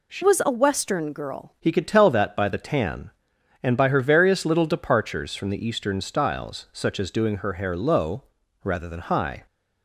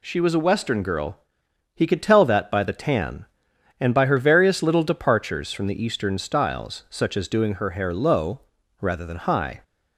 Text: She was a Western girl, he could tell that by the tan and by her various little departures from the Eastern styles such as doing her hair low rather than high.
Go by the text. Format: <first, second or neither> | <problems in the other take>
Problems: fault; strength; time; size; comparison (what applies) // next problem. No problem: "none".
second | changes voice from "was" to "girl"; from 0.2 to 1.5 s; 1.3 s long // pauses between "low" and "rather"; at 8.2 s; 0.38 s long; also in the second